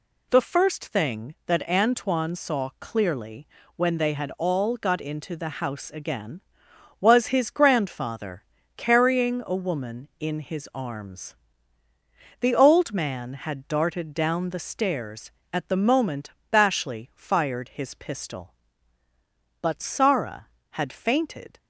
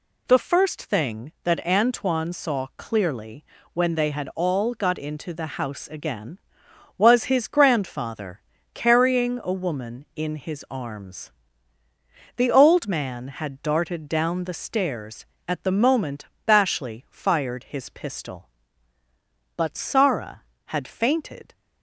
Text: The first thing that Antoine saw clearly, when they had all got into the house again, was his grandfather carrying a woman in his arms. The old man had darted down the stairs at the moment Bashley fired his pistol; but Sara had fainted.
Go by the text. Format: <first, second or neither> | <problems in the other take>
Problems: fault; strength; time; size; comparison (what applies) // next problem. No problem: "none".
neither | pauses between "grandfather" and "carrying"; slight; the same in both // pauses between "moment" and "Bashley"; slight; the same in both